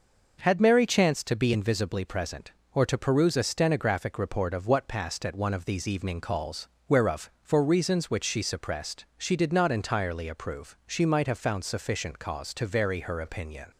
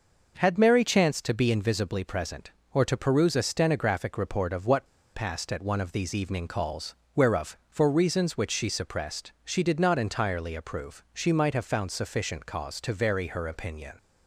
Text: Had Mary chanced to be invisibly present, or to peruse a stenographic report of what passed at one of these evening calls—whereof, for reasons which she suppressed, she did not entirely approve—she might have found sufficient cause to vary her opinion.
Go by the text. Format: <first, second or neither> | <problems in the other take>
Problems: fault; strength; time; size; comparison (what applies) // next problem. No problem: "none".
first | pauses between "what" and "passed"; slight; at 4.8 s; 0.28 s long